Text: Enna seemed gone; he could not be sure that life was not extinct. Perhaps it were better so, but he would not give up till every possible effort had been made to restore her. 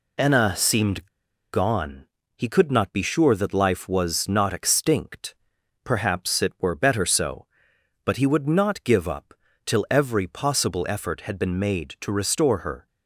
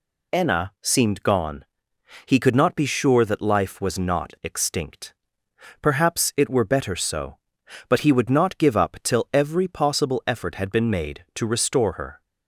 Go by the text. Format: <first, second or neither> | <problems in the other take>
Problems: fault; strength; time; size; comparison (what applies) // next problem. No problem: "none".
second | pauses between "seemed" and "gone"; at 1.0 s; 0.45 s long // pauses between "up" and "till"; slight; at 9.3 s; 0.30 s long